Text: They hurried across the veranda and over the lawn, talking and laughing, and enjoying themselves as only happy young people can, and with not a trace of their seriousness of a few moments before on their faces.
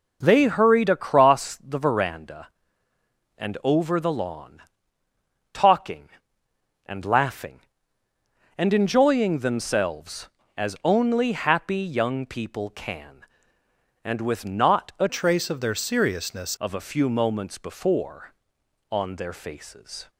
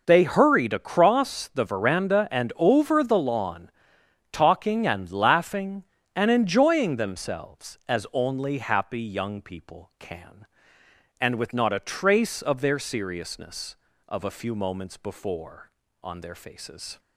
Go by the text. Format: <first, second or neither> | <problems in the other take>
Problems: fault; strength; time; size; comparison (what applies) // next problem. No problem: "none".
second | changes voice from "trace" to "seriousness"; from 15.0 to 16.5 s; 1.5 s long